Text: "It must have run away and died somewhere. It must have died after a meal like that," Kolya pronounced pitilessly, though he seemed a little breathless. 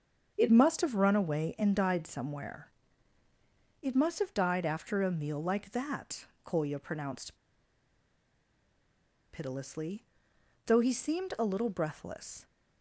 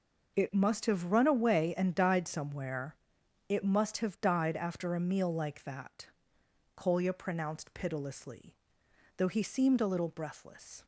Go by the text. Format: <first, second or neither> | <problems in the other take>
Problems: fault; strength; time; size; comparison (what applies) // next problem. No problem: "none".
second | starts louder than the rest; until 1.3 s; 7 dB // pauses between "pronounced" and "pitilessly"; strong; at 7.3 s; 1.9 s long